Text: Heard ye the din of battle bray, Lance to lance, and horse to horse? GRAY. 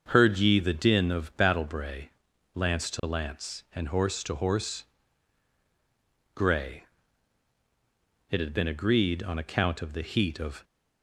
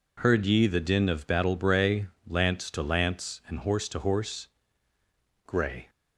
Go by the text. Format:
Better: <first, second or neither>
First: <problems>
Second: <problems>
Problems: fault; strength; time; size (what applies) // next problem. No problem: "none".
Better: second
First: starts louder than the rest; until 1.1 s; 6.5 dB // goes on to say "It had been agreed on account of the heat of"; strong; from 8.3 s on; 2.3 s long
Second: none